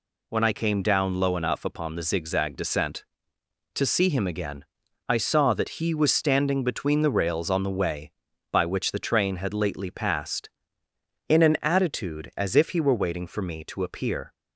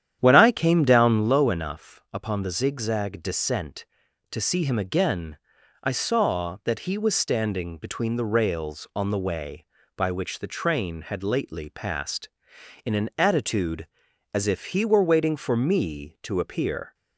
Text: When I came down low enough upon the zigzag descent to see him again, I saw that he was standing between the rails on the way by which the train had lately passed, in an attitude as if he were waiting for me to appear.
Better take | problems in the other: first | starts louder than the rest; strong; until 1.3 s; 10 dB

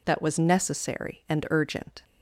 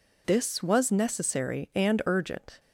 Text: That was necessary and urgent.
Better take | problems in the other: first | says "This" for "That"; at 0.2 s

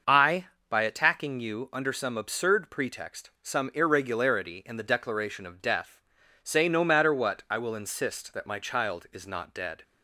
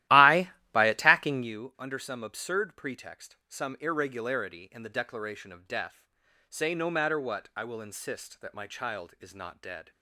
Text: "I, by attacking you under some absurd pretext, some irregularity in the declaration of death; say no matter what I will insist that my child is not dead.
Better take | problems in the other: first | starts louder than the rest; strong; until 1.5 s; 15 dB

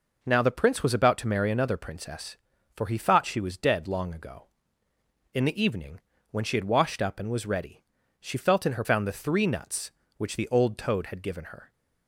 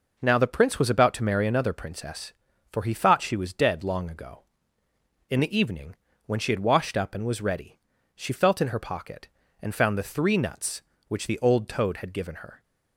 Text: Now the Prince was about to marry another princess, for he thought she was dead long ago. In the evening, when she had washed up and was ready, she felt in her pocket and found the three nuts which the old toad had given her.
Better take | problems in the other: second | skips "pocket and"; at 8.8 s

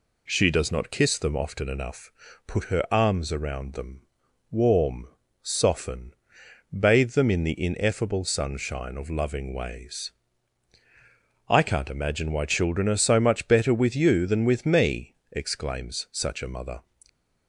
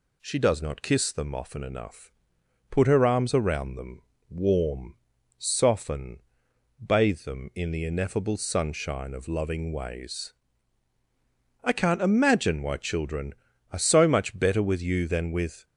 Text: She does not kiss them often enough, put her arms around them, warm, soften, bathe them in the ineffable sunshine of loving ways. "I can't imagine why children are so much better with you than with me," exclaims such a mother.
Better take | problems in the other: first | stops before "me exclaims such a mother"; at 15.6 s

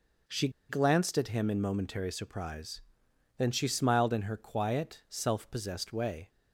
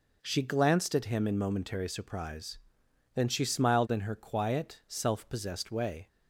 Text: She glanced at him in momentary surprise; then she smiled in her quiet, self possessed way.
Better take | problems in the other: second | pauses between "She" and "glanced"; slight; at 0.4 s; 0.19 s long

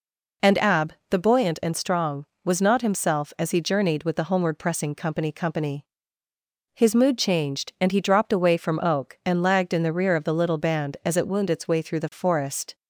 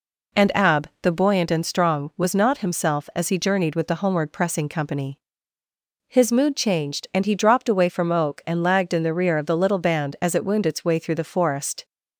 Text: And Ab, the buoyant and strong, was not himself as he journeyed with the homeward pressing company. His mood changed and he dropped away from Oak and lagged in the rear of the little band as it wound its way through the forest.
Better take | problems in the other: second | says "company" twice; at 5.3 s

